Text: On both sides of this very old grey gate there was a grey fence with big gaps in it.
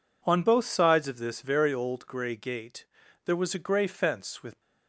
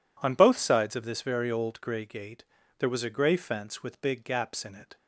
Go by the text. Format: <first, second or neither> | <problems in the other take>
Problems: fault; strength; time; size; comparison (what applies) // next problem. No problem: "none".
second | pauses between "gate" and "there"; at 2.8 s; 0.40 s long; also in the second // stops before "big gaps in it"; at 4.5 s